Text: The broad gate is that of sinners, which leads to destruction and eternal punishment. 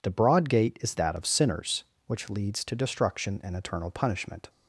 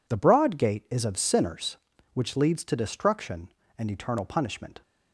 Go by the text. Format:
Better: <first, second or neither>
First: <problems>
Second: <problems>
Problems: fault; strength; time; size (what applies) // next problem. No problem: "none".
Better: first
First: none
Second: skips "that"; at 1.0 s